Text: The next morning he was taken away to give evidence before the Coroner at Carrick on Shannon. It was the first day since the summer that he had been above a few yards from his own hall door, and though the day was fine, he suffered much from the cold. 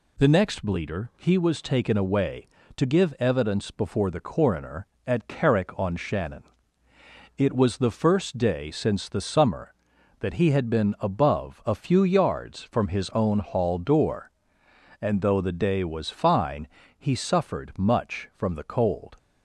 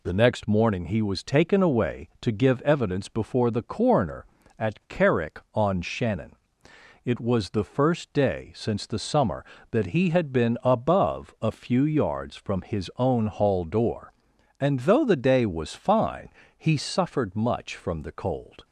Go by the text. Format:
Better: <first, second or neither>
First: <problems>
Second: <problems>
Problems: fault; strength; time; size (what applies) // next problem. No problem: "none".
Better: second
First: says "bleeder" for "morning"; at 0.6 s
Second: none